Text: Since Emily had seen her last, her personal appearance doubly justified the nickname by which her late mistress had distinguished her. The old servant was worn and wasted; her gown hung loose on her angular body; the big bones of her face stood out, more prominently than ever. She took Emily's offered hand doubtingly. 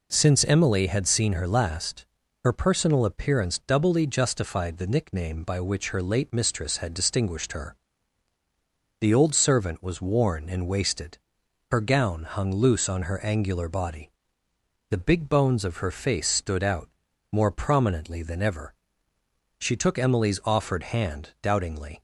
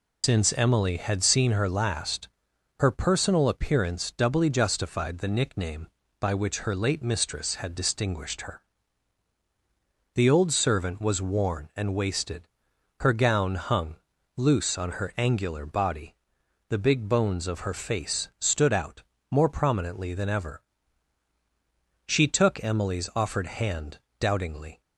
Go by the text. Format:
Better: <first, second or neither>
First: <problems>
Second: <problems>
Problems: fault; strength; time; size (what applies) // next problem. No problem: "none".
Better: first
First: none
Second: loses the start of "Since"; at 0.2 s; 85 ms // pauses between "hung" and "loose"; at 13.9 s; 0.40 s long // pauses between "hand" and "doubtingly"; slight; at 23.9 s; 0.22 s long